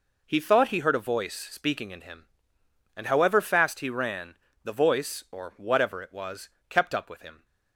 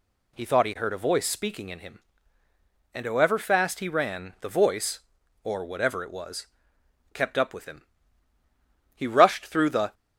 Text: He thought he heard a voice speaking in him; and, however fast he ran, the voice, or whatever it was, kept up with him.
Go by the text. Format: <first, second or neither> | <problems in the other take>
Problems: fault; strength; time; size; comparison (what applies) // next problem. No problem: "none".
first | goes on to say "He rushed through the"; noticeable; from 8.9 s on; 1.0 s long